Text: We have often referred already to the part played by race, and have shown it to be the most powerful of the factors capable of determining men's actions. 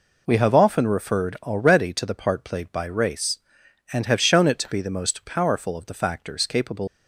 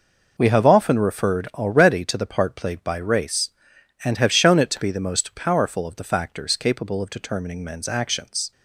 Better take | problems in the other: second | stops before "of determining men's actions"; at 6.8 s

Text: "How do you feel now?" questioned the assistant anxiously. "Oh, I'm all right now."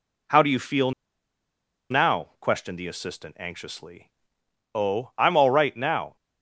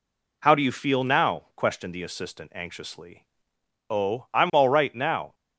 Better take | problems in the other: second | pauses between "feel" and "now"; at 0.9 s; 1.0 s long

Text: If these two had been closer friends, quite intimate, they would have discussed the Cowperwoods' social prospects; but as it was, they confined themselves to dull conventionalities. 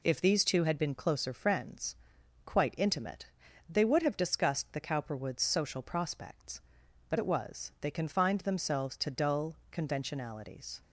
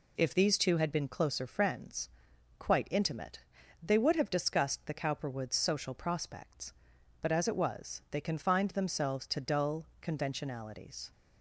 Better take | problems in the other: second | skips "as"; at 7.1 s // pauses between "dull" and "conventionalities"; slight; at 9.5 s; 0.16 s long; slight in the second

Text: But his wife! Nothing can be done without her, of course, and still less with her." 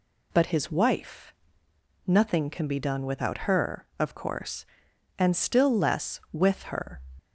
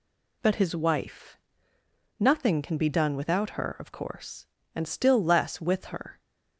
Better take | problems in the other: neither | none

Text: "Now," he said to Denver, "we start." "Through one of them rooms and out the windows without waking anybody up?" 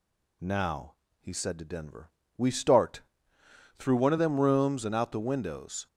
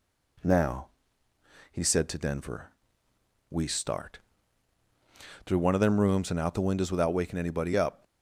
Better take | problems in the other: second | stops before "without waking anybody up"; at 5.8 s

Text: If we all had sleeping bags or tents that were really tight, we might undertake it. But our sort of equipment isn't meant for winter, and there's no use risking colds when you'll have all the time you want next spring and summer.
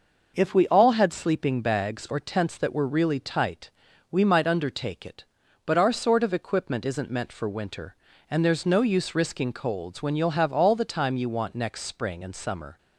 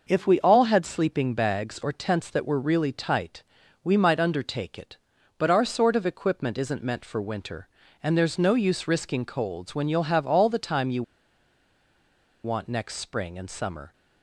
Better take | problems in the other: first | pauses between "you" and "want"; strong; at 11.0 s; 1.4 s long

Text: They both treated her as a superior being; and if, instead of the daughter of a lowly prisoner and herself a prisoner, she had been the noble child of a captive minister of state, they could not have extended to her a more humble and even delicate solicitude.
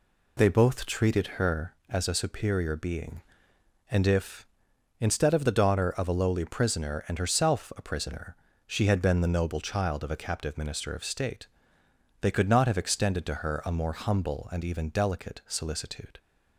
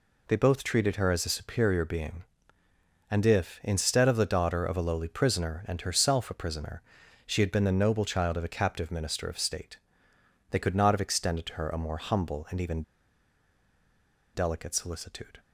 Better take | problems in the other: first | pauses between "even" and "delicate"; strong; at 12.8 s; 1.5 s long

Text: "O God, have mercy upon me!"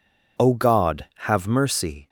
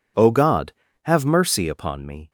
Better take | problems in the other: second | stops before "upon me"; at 2.0 s

